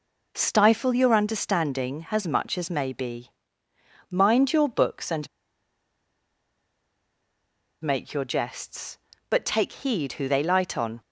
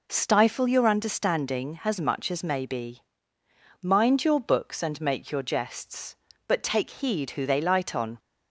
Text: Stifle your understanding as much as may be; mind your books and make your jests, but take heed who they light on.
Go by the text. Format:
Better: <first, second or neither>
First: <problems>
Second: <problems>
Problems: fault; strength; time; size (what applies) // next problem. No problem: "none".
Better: second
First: pauses between "and" and "make"; strong; at 5.2 s; 2.5 s long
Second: none